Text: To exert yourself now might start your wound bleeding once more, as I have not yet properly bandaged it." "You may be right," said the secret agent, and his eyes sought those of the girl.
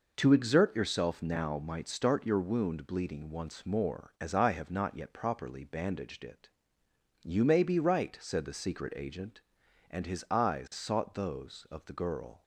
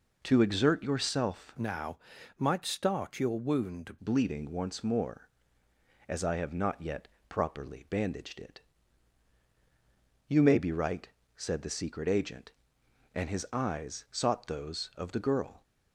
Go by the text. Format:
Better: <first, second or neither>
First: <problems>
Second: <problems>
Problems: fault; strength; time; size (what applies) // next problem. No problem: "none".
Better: first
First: none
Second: changes voice from "now" to "wound"; from 1.5 to 3.9 s; 2.4 s long // pauses between "now" and "might"; at 1.9 s; 0.40 s long // pauses between "yet" and "properly"; slight; at 7.0 s; 0.22 s long